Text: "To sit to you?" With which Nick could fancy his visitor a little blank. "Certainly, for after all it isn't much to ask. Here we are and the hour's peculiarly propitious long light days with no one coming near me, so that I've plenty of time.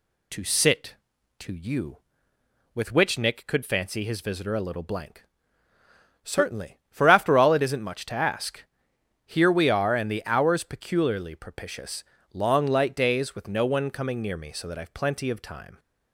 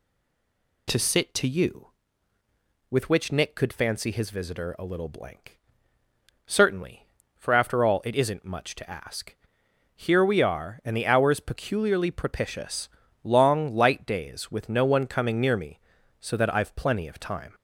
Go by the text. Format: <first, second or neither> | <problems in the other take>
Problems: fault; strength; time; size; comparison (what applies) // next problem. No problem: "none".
first | stays silent before the first word; slight; until 0.8 s; 0.8 s long // pauses between "propitious" and "long"; slight; at 12.8 s; 0.34 s long; slight in the first